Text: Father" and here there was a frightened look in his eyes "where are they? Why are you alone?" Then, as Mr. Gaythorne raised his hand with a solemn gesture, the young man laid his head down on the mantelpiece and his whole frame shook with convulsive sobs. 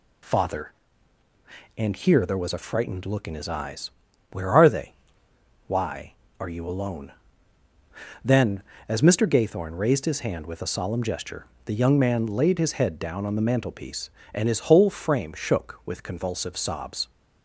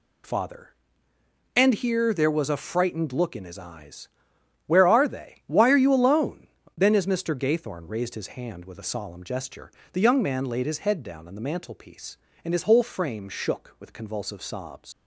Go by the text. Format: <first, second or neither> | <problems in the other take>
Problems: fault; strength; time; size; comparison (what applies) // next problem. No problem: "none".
first | pauses between "eyes" and "where"; noticeable; at 4.0 s; 0.56 s long; also in the first // leaves "sobs" unfinished; at 14.9 s; 105 ms